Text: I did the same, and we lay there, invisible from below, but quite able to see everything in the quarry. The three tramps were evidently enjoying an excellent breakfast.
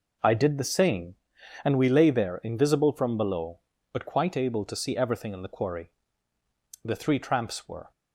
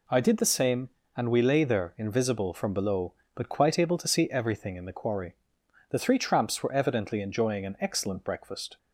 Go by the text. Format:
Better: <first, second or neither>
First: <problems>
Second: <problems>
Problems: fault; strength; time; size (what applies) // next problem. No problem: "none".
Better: second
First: stops before "evidently enjoying an excellent breakfast"; at 7.9 s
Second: none